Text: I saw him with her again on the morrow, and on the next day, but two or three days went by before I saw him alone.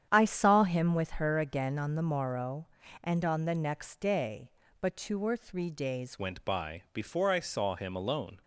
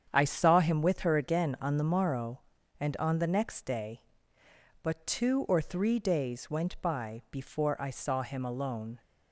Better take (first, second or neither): second